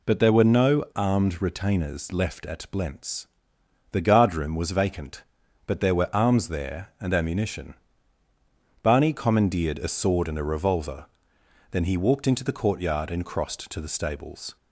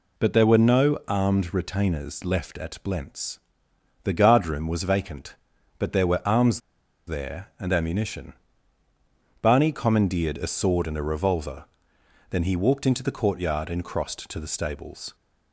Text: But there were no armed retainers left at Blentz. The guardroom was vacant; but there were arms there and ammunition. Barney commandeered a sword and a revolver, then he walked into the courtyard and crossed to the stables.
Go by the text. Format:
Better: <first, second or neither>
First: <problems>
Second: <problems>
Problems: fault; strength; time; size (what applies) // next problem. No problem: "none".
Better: first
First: none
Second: pauses between "arms" and "there"; noticeable; at 6.5 s; 0.47 s long